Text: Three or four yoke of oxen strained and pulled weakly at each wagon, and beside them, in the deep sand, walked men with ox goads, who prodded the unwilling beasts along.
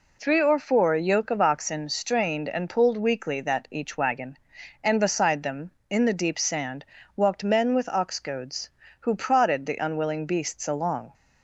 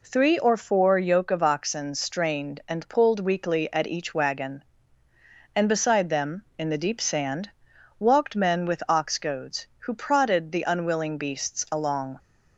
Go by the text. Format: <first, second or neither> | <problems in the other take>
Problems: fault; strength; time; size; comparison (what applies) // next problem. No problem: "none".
second | says "that" for "at"; at 3.3 s